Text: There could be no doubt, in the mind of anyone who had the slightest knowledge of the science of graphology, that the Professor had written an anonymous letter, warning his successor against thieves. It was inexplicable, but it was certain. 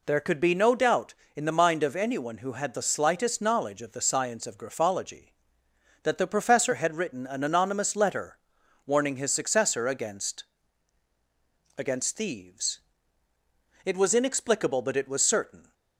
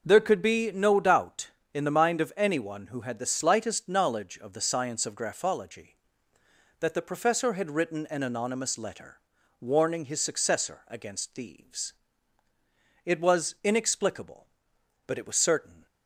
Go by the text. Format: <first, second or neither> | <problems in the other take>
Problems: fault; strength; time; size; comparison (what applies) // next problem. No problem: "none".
second | says "against" twice; at 11.7 s